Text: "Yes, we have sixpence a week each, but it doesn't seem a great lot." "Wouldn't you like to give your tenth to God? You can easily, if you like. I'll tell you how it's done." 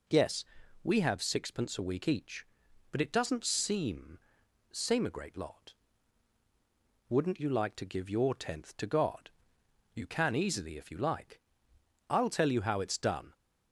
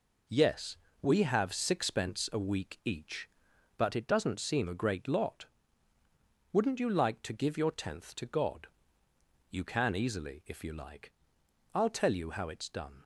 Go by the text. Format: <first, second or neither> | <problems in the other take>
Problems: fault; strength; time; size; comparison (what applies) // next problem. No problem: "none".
second | says "seem" twice; at 4.7 s